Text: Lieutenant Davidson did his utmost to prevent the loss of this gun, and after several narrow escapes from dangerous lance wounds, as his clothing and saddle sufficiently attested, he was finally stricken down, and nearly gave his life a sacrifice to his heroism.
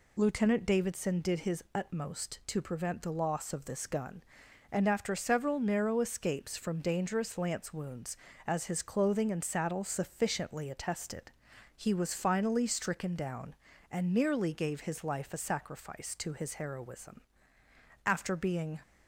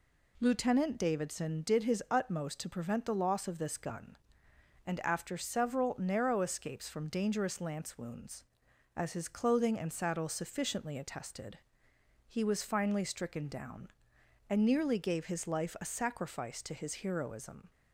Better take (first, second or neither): second